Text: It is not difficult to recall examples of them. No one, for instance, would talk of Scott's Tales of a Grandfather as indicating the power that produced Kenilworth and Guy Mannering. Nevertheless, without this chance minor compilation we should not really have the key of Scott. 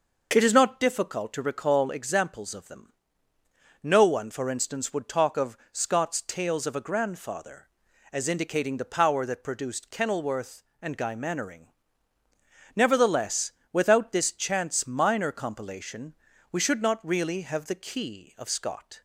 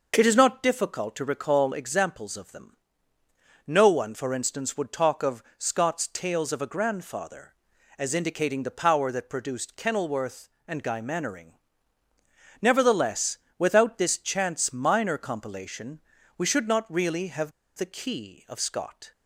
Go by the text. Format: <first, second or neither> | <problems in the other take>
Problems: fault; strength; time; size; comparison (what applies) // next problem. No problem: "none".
first | pauses between "of" and "Scott's"; slight; at 5.4 s; 0.16 s long; slight in the first // pauses between "compilation" and "we"; at 15.9 s; 0.38 s long; also in the first // pauses between "have" and "the"; slight; at 17.5 s; 0.25 s long